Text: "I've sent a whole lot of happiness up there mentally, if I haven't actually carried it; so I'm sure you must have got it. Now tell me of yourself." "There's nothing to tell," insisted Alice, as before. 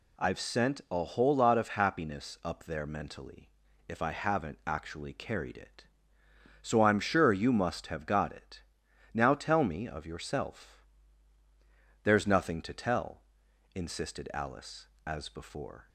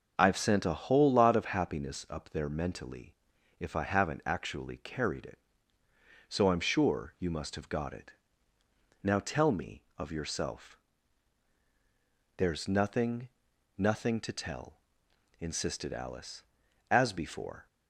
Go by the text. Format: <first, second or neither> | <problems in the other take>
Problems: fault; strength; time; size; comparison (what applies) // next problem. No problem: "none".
first | says "nothing" twice; at 13.7 s